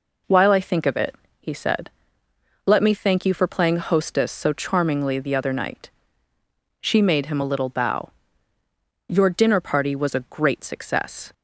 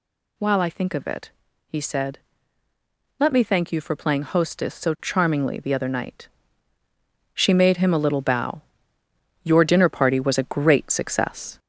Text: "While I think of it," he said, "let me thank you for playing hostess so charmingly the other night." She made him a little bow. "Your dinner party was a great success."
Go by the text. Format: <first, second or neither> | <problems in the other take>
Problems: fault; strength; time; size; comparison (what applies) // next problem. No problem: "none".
first | gets louder; throughout; 4 dB